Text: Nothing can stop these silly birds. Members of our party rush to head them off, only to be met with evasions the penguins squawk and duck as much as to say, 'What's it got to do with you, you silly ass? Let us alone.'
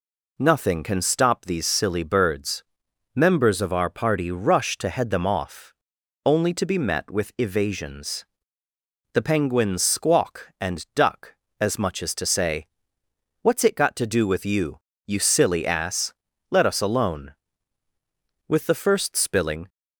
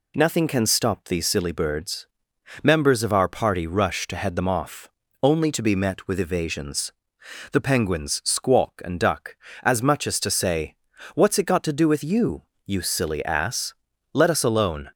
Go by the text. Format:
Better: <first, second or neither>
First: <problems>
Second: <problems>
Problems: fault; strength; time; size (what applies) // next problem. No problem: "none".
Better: second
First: pauses between "evasions" and "the"; noticeable; at 8.2 s; 0.88 s long // goes on to say "With the first spilling"; noticeable; from 18.4 s on; 1.2 s long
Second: pauses between "evasions" and "the"; noticeable; at 6.9 s; 0.60 s long